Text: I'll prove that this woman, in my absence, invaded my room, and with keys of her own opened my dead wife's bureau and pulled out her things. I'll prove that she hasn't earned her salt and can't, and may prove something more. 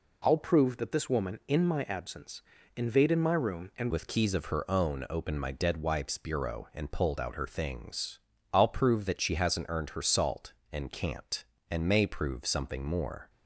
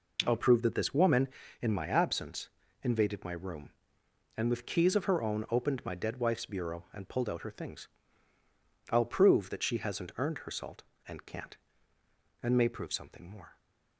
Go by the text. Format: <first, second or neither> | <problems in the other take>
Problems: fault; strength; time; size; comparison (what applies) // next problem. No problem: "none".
second | changes voice at "with"; from 3.9 s on; 9.3 s long